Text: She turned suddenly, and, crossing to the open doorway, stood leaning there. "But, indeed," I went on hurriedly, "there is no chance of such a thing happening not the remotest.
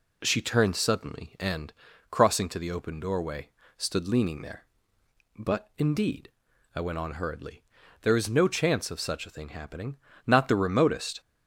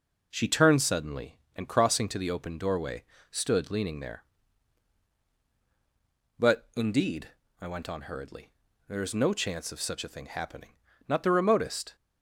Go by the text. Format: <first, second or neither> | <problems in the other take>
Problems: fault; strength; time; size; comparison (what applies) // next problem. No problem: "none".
neither | pauses between "happening" and "not"; slight; the same in both